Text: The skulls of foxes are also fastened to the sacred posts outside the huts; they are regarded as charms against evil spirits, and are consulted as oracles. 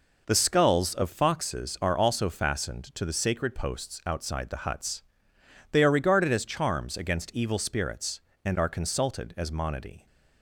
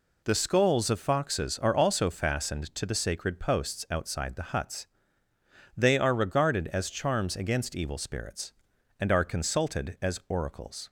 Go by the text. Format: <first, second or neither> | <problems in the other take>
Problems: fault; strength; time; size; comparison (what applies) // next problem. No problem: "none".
second | says "monody" for "oracles"; at 9.5 s